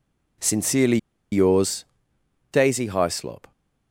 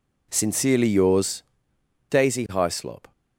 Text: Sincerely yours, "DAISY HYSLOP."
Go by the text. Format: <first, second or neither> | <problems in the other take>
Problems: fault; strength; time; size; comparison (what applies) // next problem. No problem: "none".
second | pauses between "Sincerely" and "yours"; slight; at 0.9 s; 0.34 s long